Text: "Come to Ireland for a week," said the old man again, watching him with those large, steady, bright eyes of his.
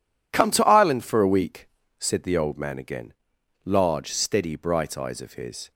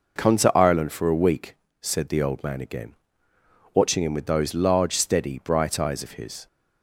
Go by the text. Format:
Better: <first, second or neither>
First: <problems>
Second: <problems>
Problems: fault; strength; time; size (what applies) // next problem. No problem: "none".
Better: second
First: skips "watching him with those"; at 3.3 s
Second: none